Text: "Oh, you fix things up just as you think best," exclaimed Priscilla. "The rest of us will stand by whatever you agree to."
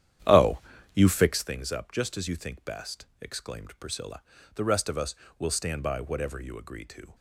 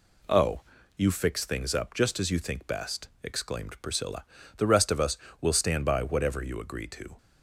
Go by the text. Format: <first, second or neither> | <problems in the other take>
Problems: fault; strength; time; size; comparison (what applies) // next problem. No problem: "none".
second | starts louder than the rest; strong; until 1.5 s; 10 dB